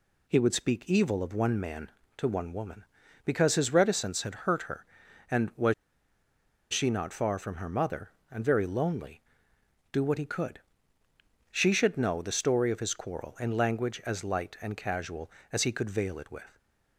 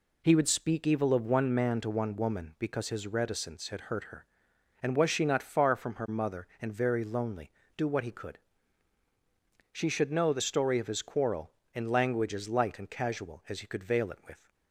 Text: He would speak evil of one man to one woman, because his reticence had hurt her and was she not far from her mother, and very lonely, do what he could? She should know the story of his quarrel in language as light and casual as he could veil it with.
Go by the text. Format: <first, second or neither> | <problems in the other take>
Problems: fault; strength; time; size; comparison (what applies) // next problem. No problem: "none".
second | pauses between "was" and "she"; noticeable; at 5.7 s; 0.97 s long